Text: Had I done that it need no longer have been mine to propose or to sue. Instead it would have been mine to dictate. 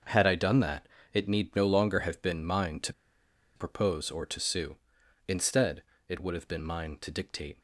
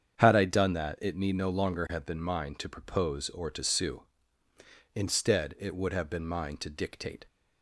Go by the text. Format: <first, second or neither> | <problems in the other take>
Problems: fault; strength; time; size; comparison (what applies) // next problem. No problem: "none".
second | starts louder than the rest; until 1.3 s; 6.5 dB; strong in the second // pauses between "that" and "it"; slight; at 0.8 s; 0.28 s long // pauses between "to" and "propose"; noticeable; at 2.9 s; 0.64 s long // pauses between "Instead" and "it"; slight; at 5.8 s; 0.24 s long